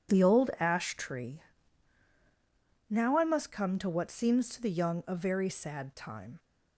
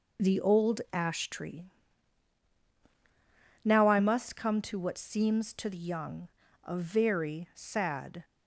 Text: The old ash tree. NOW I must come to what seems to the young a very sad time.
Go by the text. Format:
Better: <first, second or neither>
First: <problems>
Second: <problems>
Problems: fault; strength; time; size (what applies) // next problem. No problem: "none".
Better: first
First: none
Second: pauses between "young" and "a"; at 6.2 s; 0.37 s long // stops before "time"; at 8.2 s